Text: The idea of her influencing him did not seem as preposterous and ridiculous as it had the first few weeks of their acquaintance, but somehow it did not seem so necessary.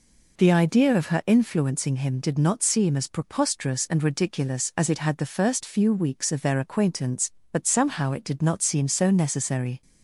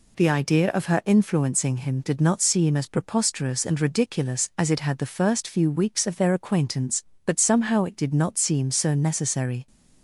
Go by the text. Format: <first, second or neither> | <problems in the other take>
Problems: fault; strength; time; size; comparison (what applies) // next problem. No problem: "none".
neither | none